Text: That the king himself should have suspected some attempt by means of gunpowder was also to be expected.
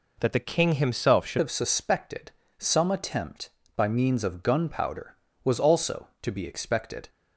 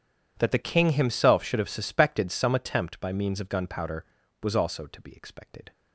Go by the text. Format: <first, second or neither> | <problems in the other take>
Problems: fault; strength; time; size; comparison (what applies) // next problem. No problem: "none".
second | changes voice at "have"; from 1.3 s on; 5.7 s long // pauses between "suspected" and "some"; slight; at 2.3 s; 0.26 s long